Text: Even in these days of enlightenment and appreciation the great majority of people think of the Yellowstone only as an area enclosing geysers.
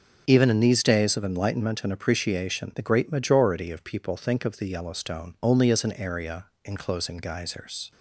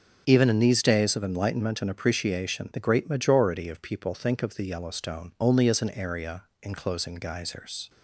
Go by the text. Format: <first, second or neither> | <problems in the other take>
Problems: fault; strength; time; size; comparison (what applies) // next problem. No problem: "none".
neither | starts louder than the rest; the same in both // pauses between "area" and "enclosing"; slight; the same in both